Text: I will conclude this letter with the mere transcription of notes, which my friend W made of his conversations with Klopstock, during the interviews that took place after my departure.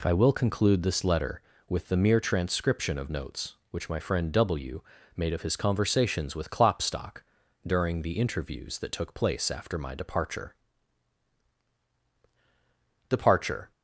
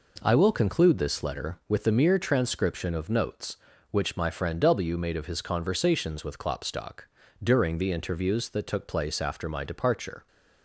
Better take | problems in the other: second | pauses between "W" and "made"; slight; at 4.8 s; 0.34 s long // says "departure" twice; at 13.0 s

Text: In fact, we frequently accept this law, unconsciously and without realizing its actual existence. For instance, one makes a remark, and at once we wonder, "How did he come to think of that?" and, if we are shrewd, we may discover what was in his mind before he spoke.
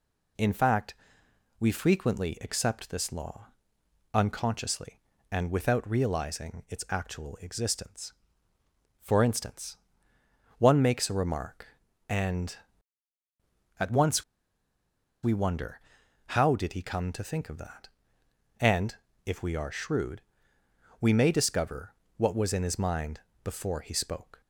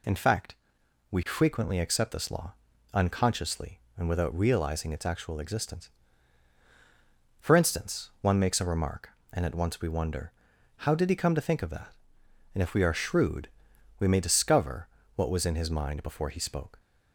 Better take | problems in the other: second | pauses between "once" and "we"; at 14.2 s; 0.99 s long // pauses between "discover" and "what"; slight; at 21.9 s; 0.24 s long; slight in the second // pauses between "mind" and "before"; slight; at 23.2 s; 0.22 s long

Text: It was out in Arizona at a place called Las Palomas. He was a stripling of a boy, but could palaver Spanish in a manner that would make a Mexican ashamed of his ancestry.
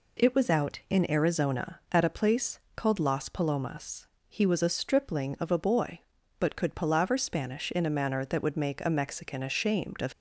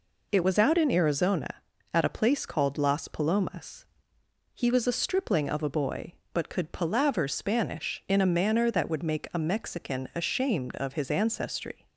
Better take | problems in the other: second | pauses between "place" and "called"; slight; at 2.5 s; 0.16 s long // stops before "his ancestry"; at 10.1 s

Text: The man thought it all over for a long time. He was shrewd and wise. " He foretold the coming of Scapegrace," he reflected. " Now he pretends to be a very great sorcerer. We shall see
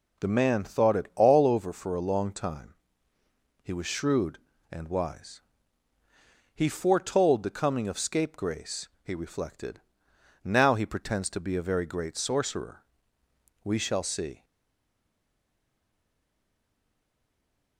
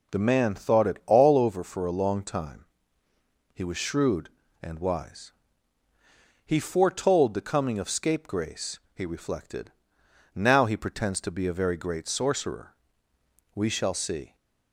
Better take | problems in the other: second | stays silent after the last word; strong; from 14.4 s on; 3.3 s long

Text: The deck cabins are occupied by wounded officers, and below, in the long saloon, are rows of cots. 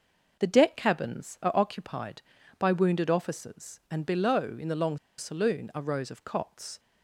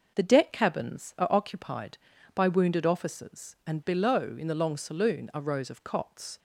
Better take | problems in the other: second | pauses between "long" and "saloon"; slight; at 4.9 s; 0.20 s long

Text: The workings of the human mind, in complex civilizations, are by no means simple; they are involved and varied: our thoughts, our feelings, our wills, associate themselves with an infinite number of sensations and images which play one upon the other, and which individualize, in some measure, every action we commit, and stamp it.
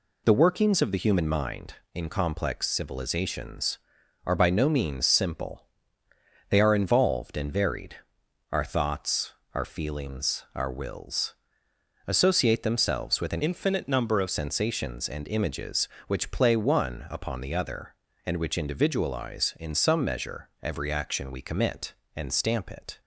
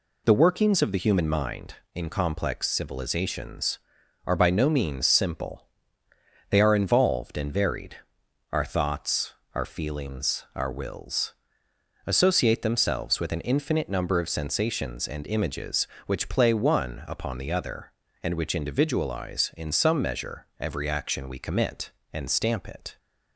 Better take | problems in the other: second | changes voice from "infinite" to "of"; from 13.4 to 14.2 s; 0.8 s long

